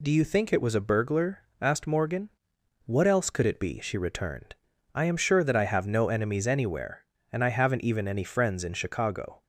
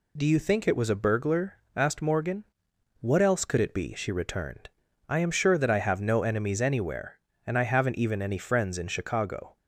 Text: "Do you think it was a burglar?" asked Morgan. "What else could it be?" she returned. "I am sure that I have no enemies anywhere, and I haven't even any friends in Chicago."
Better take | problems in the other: neither | none

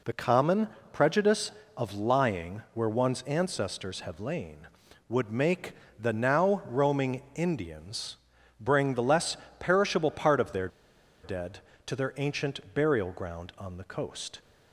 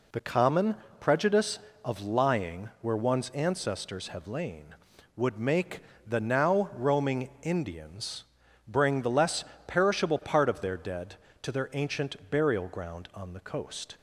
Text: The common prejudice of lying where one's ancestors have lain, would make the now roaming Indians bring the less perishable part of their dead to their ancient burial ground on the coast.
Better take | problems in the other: second | pauses between "common" and "prejudice"; slight; at 0.6 s; 0.24 s long; slight in the second // pauses between "make" and "the"; slight; at 5.7 s; 0.26 s long; slight in the second // pauses between "Indians" and "bring"; at 8.1 s; 0.44 s long; also in the second // pauses between "less" and "perishable"; slight; at 9.3 s; 0.22 s long; slight in the second // pauses between "their" and "dead"; noticeable; at 10.6 s; 0.55 s long

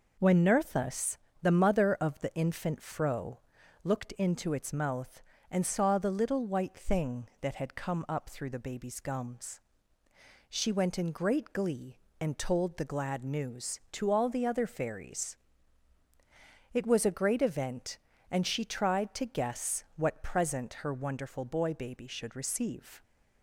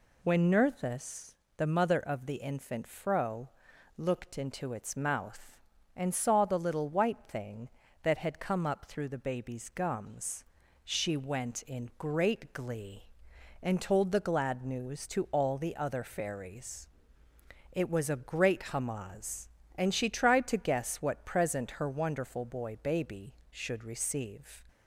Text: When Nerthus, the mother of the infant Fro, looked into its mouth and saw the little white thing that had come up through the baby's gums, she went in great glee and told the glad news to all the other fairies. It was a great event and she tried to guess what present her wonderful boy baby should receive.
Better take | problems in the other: first | says "hamaz" for "event"; at 18.7 s

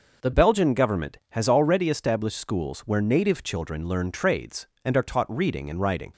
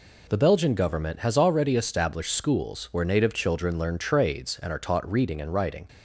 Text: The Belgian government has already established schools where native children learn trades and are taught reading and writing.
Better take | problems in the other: second | changes voice at "Belgian"; from 0.3 s on; 5.8 s long

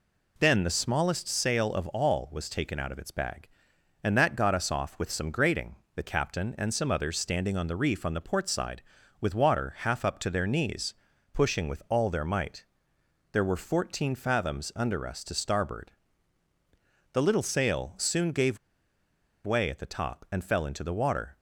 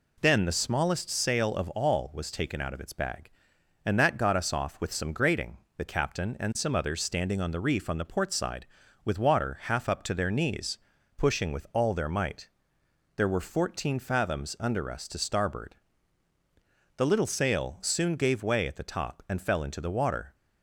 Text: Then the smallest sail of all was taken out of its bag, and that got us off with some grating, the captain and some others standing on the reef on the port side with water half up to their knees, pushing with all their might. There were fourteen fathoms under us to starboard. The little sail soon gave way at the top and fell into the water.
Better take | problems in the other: second | pauses between "gave" and "way"; noticeable; at 18.5 s; 0.87 s long

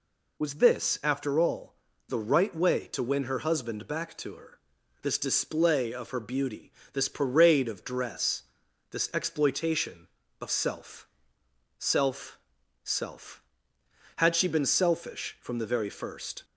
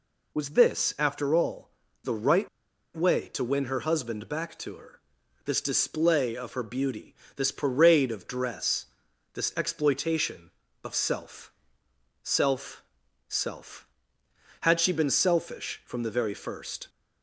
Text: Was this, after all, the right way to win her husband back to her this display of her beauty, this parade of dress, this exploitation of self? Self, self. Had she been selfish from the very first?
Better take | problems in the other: first | pauses between "right" and "way"; noticeable; at 2.4 s; 0.48 s long // pauses between "her" and "this"; noticeable; at 4.9 s; 0.50 s long; noticeable in the first

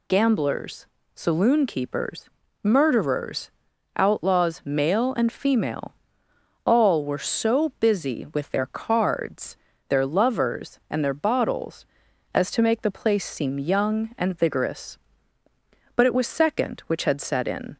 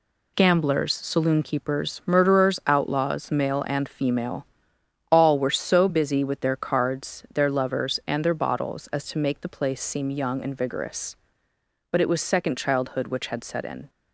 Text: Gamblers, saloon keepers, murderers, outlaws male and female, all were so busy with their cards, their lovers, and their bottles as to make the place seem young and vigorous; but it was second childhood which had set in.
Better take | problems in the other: second | skips "childhood"; at 16.8 s

